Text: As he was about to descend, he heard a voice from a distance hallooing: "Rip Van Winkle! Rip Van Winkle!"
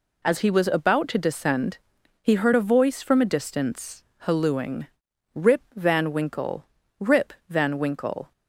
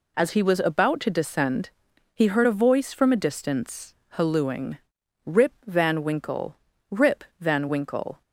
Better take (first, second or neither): neither